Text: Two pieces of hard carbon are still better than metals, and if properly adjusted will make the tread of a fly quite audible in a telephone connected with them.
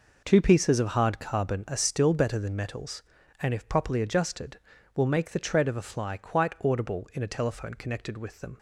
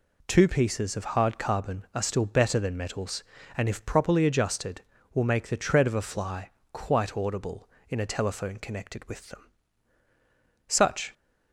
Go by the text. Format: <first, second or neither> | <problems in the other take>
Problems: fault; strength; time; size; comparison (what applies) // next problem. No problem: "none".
first | pauses between "fly" and "quite"; slight; at 6.4 s; 0.24 s long // goes on to say "Such"; slight; from 10.6 s on; 0.46 s long